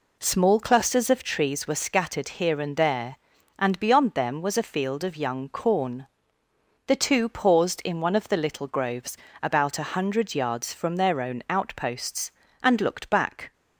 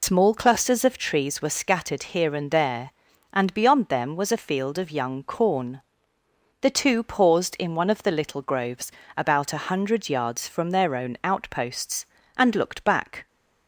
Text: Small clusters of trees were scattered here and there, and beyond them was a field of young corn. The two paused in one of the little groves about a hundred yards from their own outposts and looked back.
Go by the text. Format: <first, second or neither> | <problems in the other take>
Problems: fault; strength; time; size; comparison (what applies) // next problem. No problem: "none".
first | loses the start of "Small"; at 0.0 s; 80 ms // pauses between "groves" and "about"; slight; at 8.9 s; 0.24 s long; slight in the first